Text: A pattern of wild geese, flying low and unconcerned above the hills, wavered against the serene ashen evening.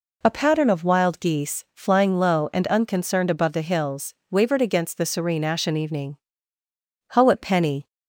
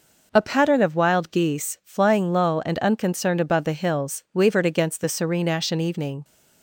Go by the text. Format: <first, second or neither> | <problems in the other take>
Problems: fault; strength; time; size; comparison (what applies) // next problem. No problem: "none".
second | goes on to say "Howat Penny"; noticeable; from 7.1 s on; 0.72 s long